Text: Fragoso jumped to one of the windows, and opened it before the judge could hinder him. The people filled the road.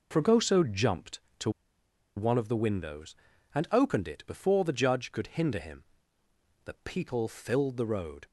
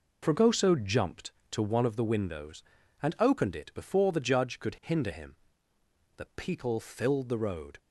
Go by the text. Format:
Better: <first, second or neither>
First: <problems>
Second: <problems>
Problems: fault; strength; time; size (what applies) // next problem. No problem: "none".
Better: second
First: pauses between "to" and "one"; noticeable; at 1.4 s; 0.66 s long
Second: none